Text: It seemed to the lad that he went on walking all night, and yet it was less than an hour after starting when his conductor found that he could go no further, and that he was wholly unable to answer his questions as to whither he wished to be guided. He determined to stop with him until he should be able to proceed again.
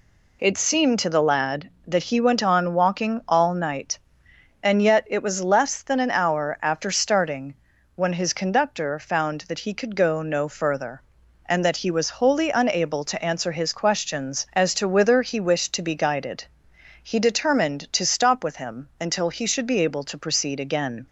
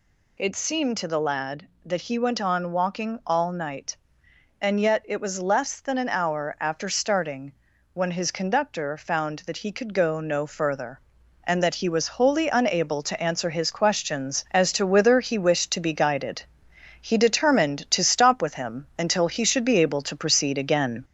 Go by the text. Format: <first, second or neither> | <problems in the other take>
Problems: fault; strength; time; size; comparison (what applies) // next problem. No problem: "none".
first | gets louder; slight; throughout; 2.5 dB // pauses between "starting" and "when"; at 7.5 s; 0.42 s long; also in the first